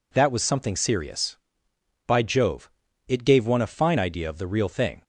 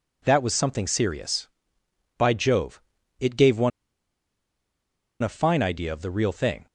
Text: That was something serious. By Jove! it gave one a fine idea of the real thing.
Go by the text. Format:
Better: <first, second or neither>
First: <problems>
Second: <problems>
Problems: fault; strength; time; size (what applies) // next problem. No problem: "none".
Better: first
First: none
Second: pauses between "one" and "a"; strong; at 3.7 s; 1.5 s long